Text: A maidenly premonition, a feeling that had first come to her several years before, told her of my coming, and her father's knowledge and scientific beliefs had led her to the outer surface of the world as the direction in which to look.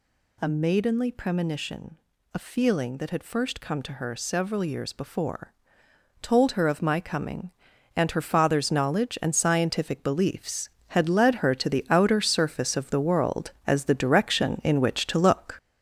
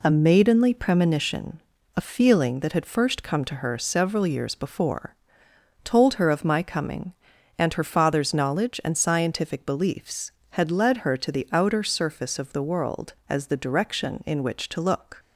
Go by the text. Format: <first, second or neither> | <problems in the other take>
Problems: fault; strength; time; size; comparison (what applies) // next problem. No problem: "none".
second | gets louder; noticeable; throughout; 6 dB